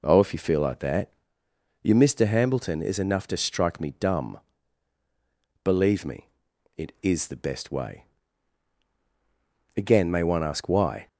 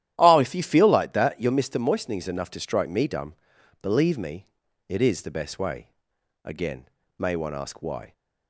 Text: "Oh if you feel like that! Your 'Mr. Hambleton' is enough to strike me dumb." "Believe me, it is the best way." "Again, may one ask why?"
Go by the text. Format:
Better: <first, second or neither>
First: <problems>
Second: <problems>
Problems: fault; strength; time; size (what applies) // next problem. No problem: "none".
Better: first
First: none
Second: starts louder than the rest; strong; until 1.1 s; 12 dB // says "Moistening" for "Hambleton"; at 1.7 s